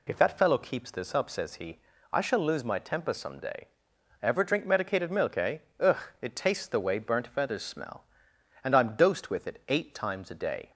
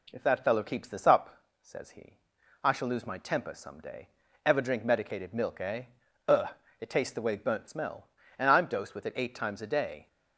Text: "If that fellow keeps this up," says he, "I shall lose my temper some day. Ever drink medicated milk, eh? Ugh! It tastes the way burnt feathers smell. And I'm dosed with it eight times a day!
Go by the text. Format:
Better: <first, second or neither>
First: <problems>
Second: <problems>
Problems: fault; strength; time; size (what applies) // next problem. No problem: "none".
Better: first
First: none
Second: skips "feathers"; at 7.6 s